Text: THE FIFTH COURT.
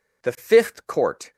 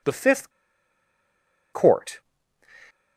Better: first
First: none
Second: pauses between "FIFTH" and "COURT"; at 0.5 s; 1.2 s long

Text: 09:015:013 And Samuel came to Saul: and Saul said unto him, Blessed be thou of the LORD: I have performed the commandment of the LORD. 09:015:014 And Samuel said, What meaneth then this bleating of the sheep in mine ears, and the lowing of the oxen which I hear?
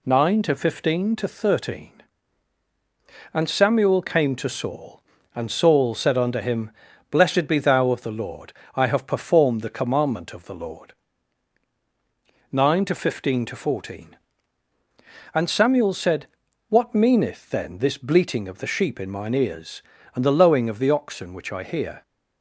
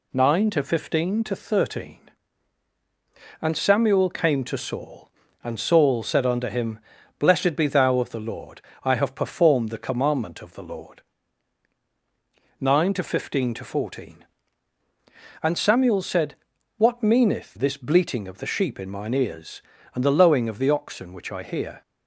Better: first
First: none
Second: skips "then"; at 17.5 s

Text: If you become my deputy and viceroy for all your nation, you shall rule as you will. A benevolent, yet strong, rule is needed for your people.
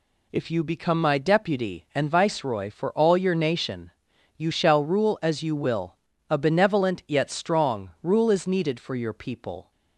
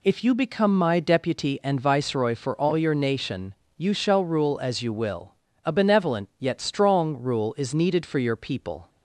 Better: neither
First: none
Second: none

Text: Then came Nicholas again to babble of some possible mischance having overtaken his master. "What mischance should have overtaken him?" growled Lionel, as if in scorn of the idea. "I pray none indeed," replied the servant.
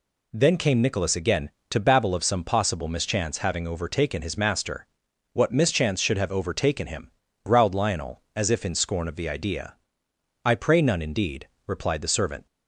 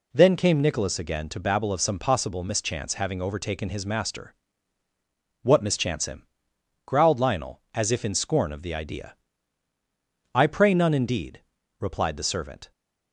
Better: first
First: none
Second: skips "should have overtaken"; at 6.0 s

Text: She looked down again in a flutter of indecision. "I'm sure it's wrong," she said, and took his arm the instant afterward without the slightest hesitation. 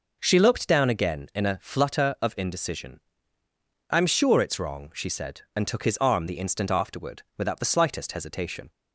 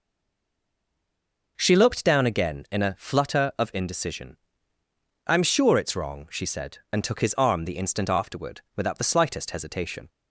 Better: first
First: none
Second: stays silent before the first word; noticeable; until 1.5 s; 1.5 s long

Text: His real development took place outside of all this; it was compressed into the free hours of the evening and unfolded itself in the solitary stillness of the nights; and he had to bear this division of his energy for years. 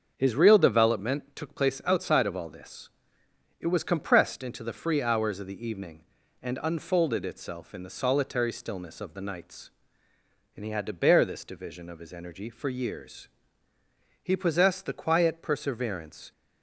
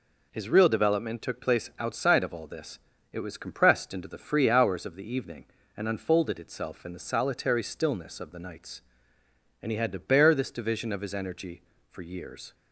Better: second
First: starts louder than the rest; until 1.1 s; 6.5 dB // goes on to say "He possessed the quiet perseverance"; strong; from 14.2 s on; 2.1 s long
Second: none

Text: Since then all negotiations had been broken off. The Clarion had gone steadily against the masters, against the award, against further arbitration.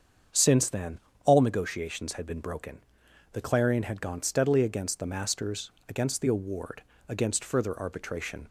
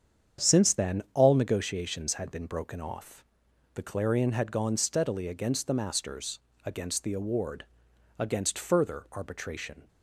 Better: second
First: starts louder than the rest; strong; until 1.5 s; 7.5 dB // pauses between "then" and "all"; slight; at 0.9 s; 0.26 s long // skips "off"; at 3.0 s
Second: starts louder than the rest; strong; until 1.5 s; 8 dB

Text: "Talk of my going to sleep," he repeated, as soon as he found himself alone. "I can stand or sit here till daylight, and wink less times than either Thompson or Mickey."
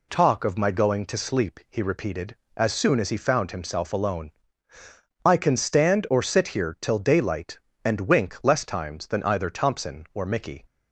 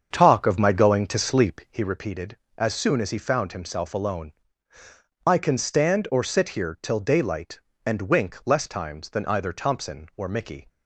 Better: first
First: none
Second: starts louder than the rest; until 1.9 s; 7 dB

